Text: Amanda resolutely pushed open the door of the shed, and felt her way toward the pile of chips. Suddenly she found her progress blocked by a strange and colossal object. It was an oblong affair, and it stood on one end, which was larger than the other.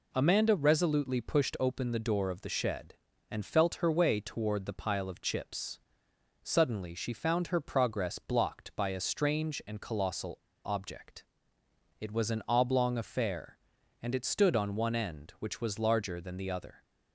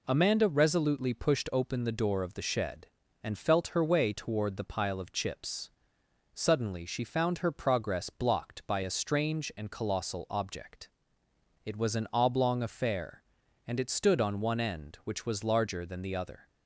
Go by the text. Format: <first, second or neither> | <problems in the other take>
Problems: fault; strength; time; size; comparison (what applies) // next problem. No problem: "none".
second | pauses between "colossal" and "object"; slight; at 10.3 s; 0.29 s long